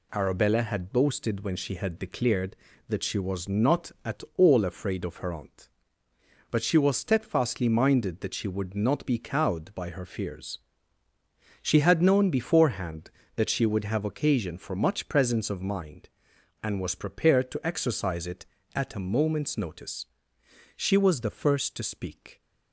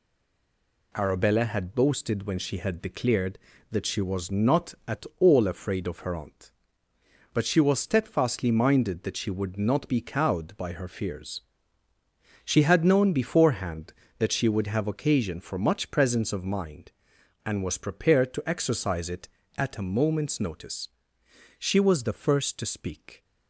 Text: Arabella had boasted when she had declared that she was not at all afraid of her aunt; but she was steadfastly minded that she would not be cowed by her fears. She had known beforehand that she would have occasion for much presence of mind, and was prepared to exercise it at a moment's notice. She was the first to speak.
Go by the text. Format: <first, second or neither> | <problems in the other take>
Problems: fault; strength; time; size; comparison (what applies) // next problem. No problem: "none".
first | stays silent before the first word; slight; until 0.9 s; 0.9 s long